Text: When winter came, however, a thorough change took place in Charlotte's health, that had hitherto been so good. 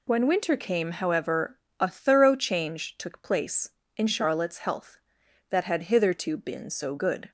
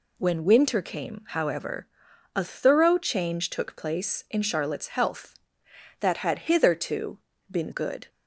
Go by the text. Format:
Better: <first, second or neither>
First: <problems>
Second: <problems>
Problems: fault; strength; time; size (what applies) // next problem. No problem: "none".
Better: first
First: none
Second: pauses between "hitherto" and "been"; slight; at 7.1 s; 0.32 s long // skips "so"; at 7.7 s